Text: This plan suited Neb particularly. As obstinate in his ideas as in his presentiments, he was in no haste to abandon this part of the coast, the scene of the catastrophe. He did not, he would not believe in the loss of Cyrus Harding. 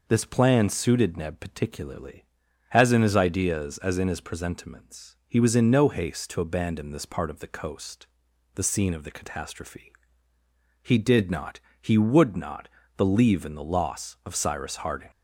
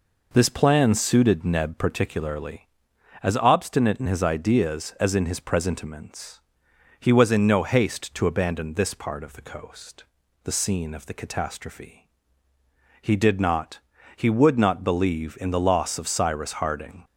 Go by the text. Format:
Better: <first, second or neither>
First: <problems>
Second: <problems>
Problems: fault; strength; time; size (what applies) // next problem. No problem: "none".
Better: second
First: skips "obstinate"; at 2.9 s // pauses between "not" and "believe"; slight; at 12.6 s; 0.28 s long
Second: none